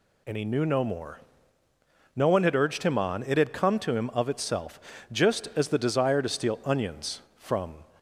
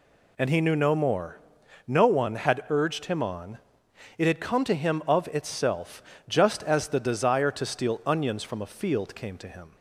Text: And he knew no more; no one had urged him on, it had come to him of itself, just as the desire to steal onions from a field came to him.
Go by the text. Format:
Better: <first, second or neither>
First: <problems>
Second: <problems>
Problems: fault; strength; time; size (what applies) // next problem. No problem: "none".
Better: second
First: stops before "a field came to him"; at 7.9 s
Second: none